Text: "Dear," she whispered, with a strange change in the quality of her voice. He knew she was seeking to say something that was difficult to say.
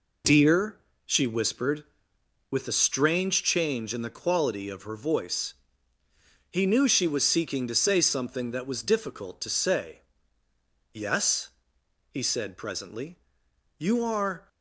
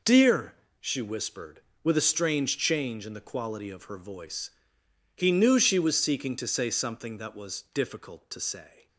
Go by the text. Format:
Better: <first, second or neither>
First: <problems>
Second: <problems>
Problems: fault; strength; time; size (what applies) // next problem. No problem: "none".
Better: second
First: goes on to say "Yes he said presently You are"; strong; from 10.9 s on; 3.5 s long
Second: none